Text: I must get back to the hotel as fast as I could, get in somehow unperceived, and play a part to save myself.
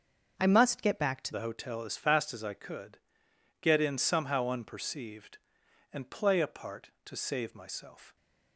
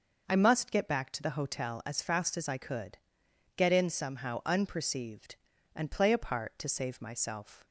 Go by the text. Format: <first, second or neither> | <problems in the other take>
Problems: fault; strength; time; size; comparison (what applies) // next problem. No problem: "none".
second | starts louder than the rest; until 1.3 s; 6.5 dB // changes voice at "the"; from 1.3 s on; 6.8 s long